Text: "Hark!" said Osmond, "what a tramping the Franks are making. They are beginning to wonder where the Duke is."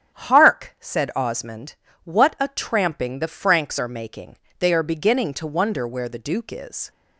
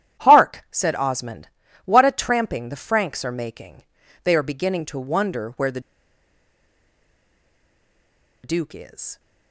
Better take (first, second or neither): first